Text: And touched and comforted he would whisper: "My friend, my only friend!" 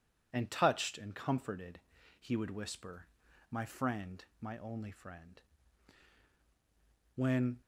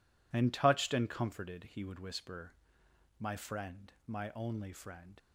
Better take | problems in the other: second | pauses between "comforted" and "he"; at 1.7 s; 0.40 s long // goes on to say "When"; slight; from 7.1 s on; 0.46 s long

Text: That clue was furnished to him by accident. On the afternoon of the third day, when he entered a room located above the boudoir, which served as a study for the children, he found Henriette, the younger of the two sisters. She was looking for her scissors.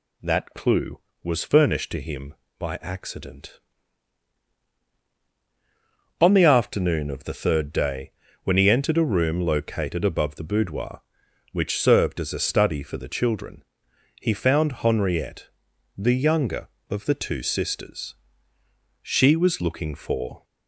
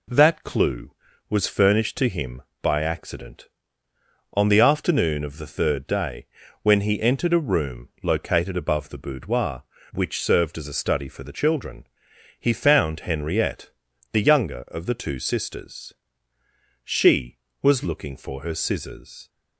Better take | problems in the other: second | stops before "her scissors"; at 20.4 s

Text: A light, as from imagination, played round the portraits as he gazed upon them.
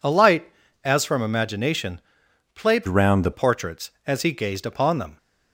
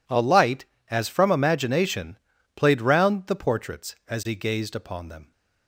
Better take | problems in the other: second | changes voice from "round" to "the"; from 2.8 to 3.3 s; 0.5 s long

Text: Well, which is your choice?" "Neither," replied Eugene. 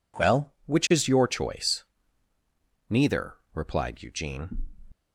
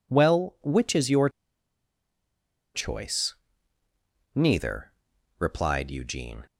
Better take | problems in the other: first | pauses between "your" and "choice"; strong; at 1.2 s; 1.4 s long

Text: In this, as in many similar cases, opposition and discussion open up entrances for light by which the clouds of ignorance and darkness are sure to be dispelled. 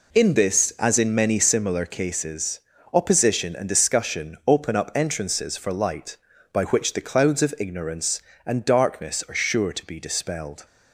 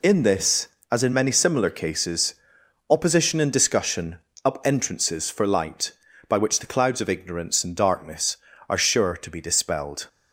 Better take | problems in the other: first | skips "open"; at 4.3 s

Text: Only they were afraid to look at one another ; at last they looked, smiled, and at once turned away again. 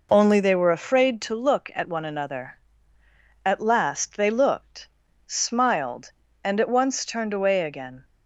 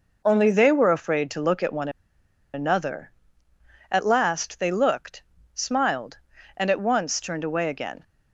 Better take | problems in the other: first | pauses between "one" and "another"; noticeable; at 1.8 s; 0.65 s long

